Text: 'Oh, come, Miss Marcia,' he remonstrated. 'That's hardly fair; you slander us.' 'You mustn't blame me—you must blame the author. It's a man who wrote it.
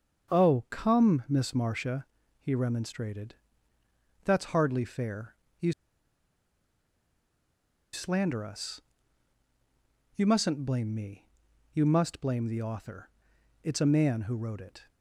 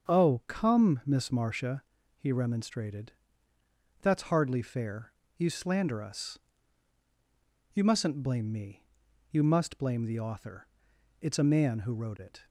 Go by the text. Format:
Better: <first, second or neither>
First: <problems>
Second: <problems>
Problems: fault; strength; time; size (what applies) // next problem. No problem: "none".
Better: second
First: starts louder than the rest; until 1.4 s; 7 dB // pauses between "you" and "slander"; strong; at 5.7 s; 2.2 s long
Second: starts louder than the rest; until 1.1 s; 7 dB